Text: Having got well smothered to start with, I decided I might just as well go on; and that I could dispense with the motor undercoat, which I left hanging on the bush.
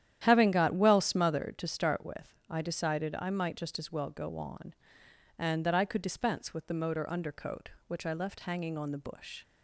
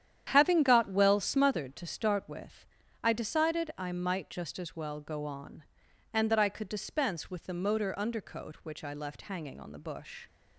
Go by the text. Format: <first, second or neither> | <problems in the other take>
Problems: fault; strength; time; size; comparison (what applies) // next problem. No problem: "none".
neither | starts louder than the rest; strong; the same in both